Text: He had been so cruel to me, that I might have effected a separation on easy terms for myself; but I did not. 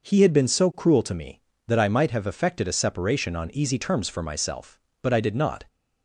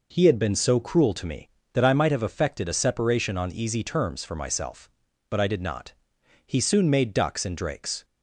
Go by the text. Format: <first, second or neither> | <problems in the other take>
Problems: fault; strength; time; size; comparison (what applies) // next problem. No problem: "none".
first | goes on to say "He soon made ducks and drakes"; from 6.4 s on; 1.5 s long